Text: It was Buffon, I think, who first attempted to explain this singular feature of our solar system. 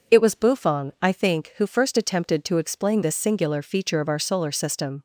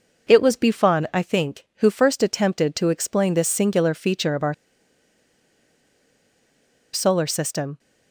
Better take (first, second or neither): first